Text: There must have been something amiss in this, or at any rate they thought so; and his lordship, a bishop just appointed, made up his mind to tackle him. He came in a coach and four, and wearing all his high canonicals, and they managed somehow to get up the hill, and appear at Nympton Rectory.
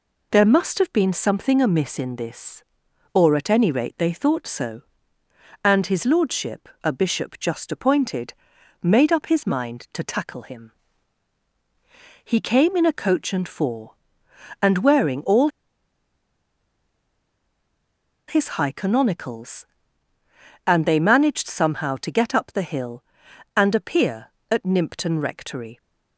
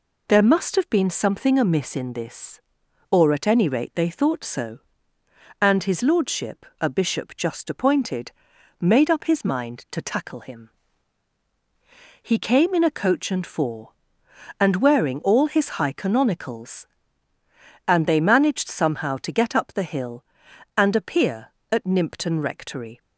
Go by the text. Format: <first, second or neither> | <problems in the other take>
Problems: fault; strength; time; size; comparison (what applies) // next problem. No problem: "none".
second | pauses between "all" and "his"; strong; at 15.4 s; 2.7 s long